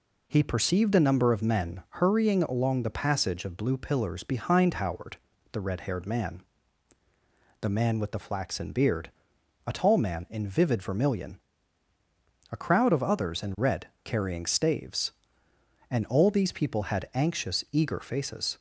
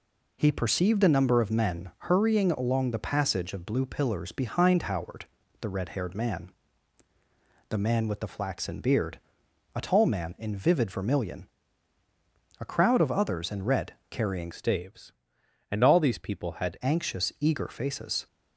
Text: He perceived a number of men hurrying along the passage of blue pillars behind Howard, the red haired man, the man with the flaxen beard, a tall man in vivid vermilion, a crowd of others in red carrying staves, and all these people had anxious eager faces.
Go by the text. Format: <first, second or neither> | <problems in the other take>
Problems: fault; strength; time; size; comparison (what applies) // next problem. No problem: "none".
first | pauses between "red" and "carrying"; slight; at 13.9 s; 0.16 s long; slight in the first // changes voice from "staves" to "had"; from 14.5 to 16.7 s; 2.2 s long